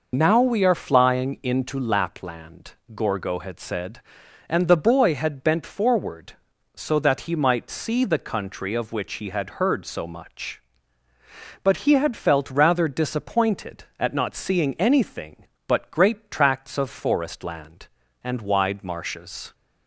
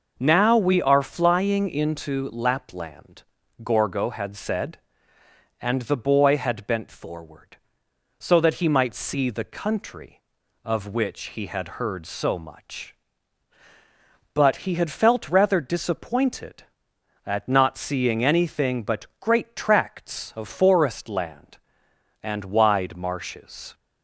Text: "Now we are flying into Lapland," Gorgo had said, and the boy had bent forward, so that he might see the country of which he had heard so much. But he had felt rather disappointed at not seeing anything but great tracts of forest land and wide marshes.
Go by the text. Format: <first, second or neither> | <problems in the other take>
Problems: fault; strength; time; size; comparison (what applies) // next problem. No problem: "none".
second | loses the start of "Now"; at 0.1 s; 55 ms